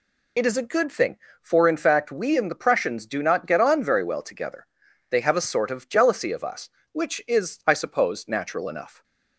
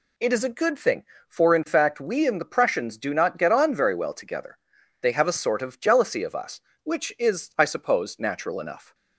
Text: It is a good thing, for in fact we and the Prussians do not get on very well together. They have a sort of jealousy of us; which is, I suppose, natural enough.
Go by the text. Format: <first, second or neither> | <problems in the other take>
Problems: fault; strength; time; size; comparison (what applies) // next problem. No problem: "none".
second | loses the start of "It"; at 0.3 s; 50 ms